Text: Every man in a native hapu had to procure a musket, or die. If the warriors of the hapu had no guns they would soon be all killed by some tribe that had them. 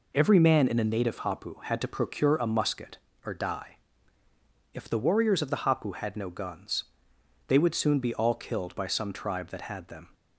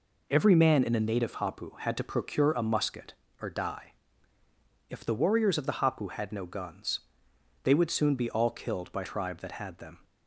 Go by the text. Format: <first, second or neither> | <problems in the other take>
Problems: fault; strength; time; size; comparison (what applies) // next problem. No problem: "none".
first | pauses between "guns" and "they"; noticeable; at 7.0 s; 0.64 s long; noticeable in the first // skips "some"; at 9.0 s